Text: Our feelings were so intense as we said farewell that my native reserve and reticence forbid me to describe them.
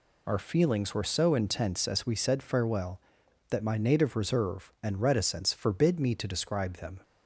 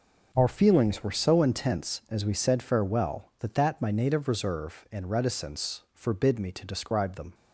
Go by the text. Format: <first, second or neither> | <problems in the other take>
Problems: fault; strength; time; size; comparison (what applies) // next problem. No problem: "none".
first | says "that" twice; at 3.5 s